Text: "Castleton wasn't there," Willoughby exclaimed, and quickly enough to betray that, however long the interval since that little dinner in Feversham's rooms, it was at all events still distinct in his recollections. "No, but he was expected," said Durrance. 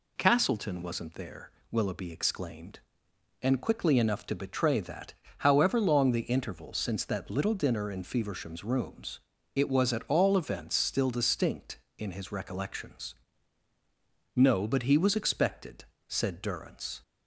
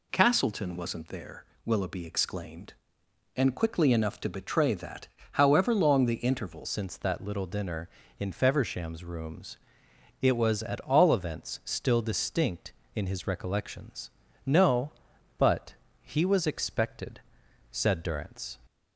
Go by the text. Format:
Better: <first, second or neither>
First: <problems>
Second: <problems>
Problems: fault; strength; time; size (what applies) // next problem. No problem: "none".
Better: first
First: none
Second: changes voice at "since"; from 6.6 s on; 11.9 s long // pauses between "but" and "he"; slight; at 15.7 s; 0.30 s long